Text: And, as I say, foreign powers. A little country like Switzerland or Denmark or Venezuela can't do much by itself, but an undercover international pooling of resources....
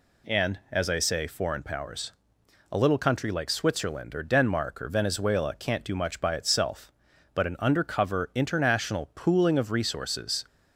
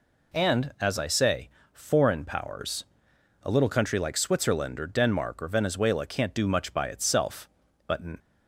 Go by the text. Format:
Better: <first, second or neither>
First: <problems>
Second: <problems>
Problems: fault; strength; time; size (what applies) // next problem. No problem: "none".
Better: first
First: none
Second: stops before "undercover international pooling of resources"; at 8.1 s